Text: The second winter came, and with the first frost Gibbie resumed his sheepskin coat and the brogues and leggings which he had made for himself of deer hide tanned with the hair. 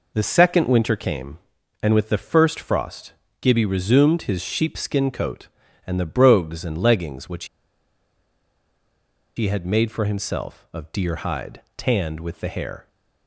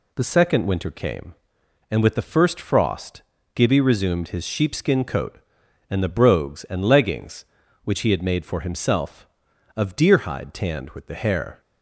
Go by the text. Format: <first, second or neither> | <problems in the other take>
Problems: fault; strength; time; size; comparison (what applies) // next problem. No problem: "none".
second | pauses between "frost" and "Gibbie"; slight; at 3.1 s; 0.28 s long; slight in the second // pauses between "which" and "he"; strong; at 7.4 s; 1.9 s long